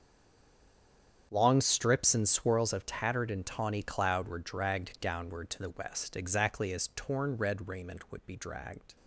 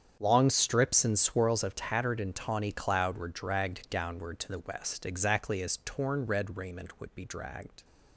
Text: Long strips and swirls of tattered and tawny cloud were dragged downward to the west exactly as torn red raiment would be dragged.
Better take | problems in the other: second | stays silent before the first word; noticeable; until 1.3 s; 1.3 s long // starts louder than the rest; strong; until 2.3 s; 8 dB; strong in the second

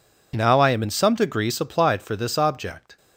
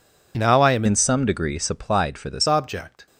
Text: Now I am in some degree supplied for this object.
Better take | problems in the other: first | changes voice from "in" to "this"; from 0.8 to 2.4 s; 1.6 s long

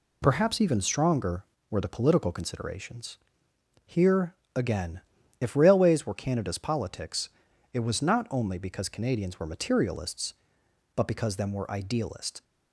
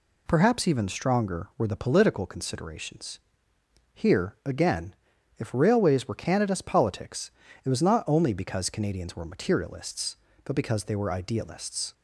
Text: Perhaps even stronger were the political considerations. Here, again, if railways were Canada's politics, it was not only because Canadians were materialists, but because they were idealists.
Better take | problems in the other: second | says "them" for "they"; at 11.3 s

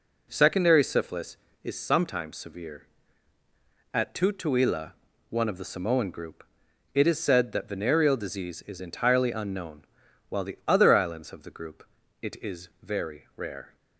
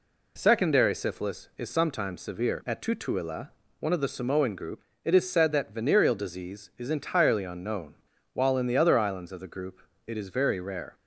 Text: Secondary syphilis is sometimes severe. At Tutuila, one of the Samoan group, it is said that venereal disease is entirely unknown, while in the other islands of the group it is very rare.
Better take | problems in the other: second | skips "in"; at 10.4 s // pauses between "group" and "it"; slight; at 11.8 s; 0.36 s long; slight in the second // pauses between "is" and "very"; slight; at 12.6 s; 0.16 s long

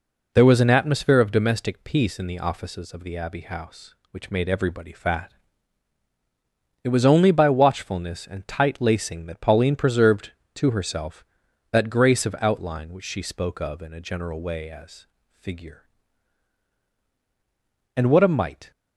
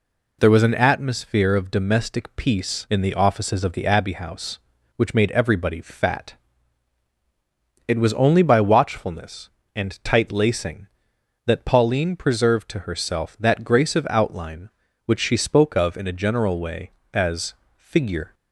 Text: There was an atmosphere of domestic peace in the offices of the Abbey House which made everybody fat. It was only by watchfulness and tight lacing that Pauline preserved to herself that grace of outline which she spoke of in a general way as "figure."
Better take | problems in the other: second | pauses between "as" and "figure"; slight; at 15.0 s; 0.26 s long; slight in the second // goes on to say "And what a mite"; noticeable; from 17.9 s on; 0.76 s long

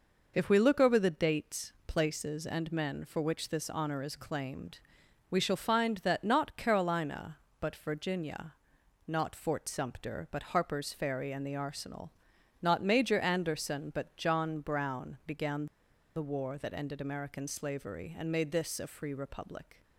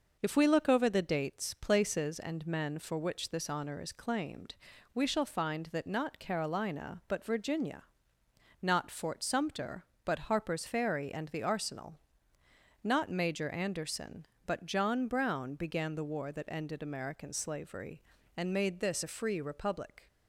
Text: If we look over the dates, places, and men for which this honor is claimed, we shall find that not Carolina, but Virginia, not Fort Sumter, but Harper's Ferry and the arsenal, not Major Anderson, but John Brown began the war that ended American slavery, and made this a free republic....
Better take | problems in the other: second | pauses between "began" and "the"; noticeable; at 15.6 s; 0.49 s long

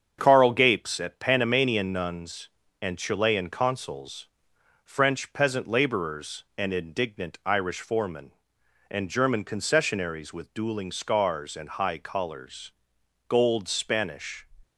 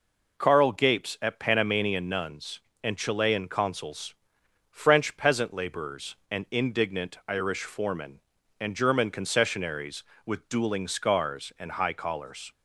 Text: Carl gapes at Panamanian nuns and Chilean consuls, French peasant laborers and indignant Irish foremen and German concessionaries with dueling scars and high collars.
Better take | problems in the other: second | starts louder than the rest; strong; until 1.2 s; 7 dB // goes on to say "Gold Spanish"; noticeable; from 13.2 s on; 1.1 s long

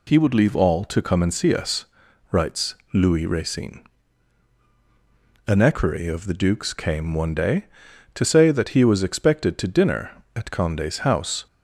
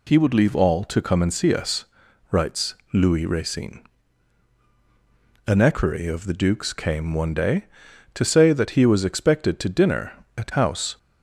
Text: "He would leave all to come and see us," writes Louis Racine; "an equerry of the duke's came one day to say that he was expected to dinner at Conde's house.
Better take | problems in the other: first | pauses between "writes" and "Louis"; slight; at 2.7 s; 0.18 s long; slight in the first // skips "Conde's"; at 10.5 s

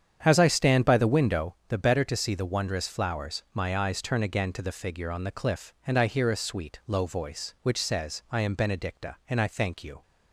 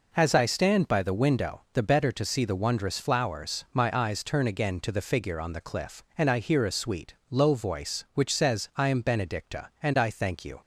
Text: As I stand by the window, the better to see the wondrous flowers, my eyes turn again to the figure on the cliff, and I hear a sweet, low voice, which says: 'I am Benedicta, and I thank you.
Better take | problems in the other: second | starts louder than the rest; strong; until 1.6 s; 8.5 dB

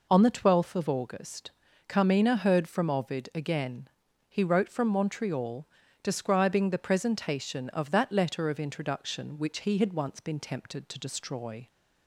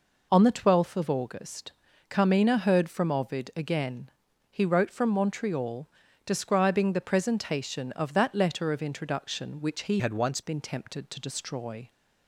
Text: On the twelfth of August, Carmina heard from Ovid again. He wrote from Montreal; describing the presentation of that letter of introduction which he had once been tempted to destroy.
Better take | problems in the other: first | changes voice from "had" to "once"; from 9.9 to 10.4 s; 0.5 s long

